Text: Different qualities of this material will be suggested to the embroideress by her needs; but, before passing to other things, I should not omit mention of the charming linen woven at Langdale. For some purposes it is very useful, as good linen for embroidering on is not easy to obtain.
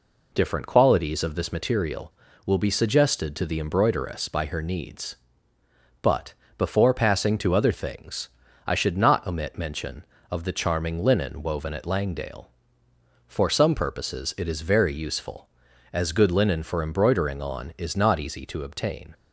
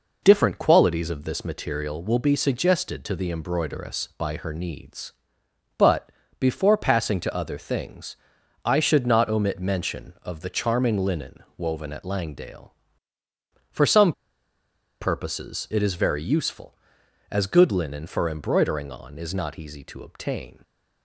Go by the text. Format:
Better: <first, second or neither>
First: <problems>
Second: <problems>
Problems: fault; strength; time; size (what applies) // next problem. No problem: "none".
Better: first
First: none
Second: pauses between "some" and "purposes"; noticeable; at 14.1 s; 0.87 s long